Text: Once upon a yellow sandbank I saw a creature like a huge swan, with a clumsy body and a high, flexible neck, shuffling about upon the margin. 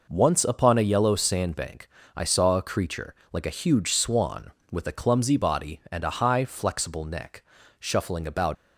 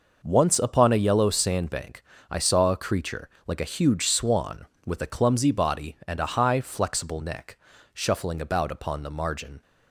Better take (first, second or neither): second